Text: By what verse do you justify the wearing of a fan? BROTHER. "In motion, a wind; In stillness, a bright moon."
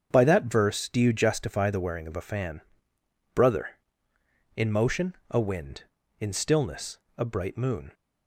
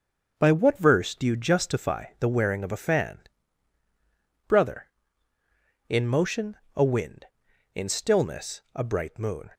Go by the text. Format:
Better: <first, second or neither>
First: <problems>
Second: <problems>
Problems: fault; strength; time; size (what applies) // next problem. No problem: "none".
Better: second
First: starts louder than the rest; strong; until 1.1 s; 7.5 dB // says "that" for "what"; at 0.2 s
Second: starts louder than the rest; until 1.3 s; 6.5 dB